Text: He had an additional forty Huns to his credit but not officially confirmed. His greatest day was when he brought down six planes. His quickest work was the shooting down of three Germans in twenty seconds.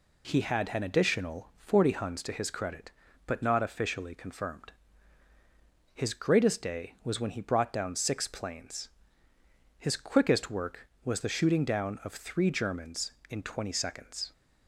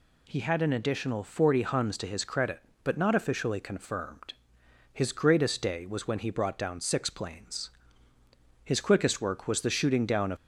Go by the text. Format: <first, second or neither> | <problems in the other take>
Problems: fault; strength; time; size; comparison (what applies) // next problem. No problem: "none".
first | stops before "three Germans in twenty seconds"; at 10.3 s